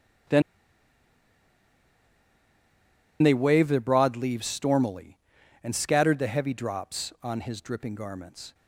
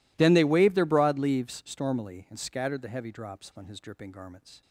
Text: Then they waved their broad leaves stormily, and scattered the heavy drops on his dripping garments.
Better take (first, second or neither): second